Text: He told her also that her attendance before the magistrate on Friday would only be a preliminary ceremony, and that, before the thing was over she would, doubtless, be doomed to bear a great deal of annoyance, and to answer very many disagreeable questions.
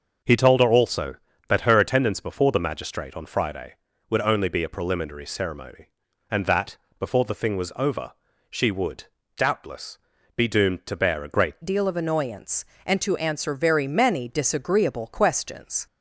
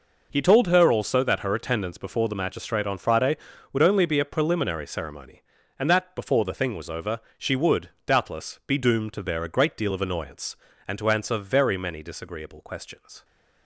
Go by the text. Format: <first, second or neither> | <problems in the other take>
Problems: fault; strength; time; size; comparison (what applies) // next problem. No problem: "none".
second | starts louder than the rest; until 1.5 s; 6 dB // pauses between "over" and "she"; at 8.1 s; 0.40 s long; slight in the second // changes voice at "deal"; from 11.6 s on; 4.2 s long